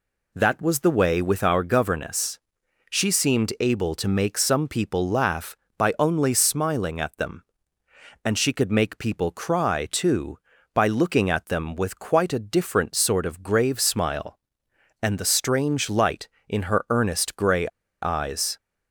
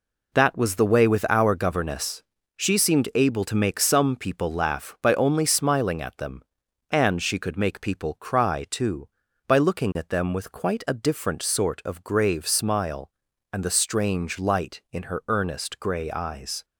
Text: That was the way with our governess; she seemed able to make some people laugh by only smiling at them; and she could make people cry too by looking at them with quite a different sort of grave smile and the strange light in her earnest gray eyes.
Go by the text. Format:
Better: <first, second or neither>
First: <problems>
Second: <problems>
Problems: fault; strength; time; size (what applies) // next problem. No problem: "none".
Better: second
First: pauses between "gray" and "eyes"; slight; at 17.6 s; 0.33 s long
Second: none